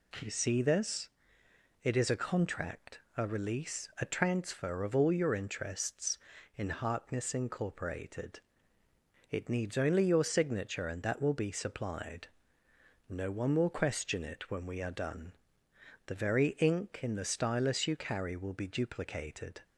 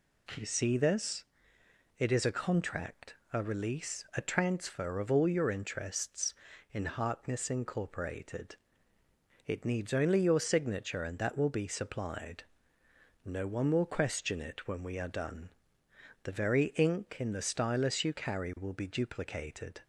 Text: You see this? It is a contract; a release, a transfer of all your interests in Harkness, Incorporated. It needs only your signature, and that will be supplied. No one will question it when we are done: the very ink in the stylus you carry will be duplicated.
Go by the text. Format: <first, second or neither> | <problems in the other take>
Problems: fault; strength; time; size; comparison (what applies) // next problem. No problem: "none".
neither | none